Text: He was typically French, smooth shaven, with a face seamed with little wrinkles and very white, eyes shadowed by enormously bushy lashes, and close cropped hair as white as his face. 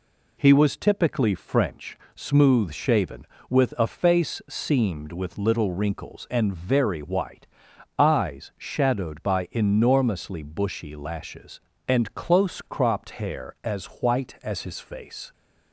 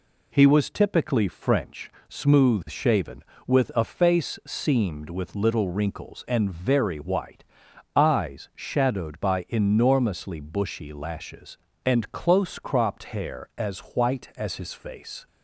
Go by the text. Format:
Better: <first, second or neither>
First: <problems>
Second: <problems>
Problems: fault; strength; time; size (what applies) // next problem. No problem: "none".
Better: neither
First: none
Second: none